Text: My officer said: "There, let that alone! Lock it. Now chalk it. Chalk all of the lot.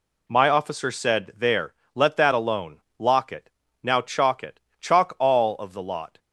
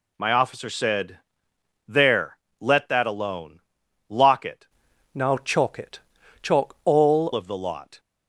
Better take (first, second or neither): first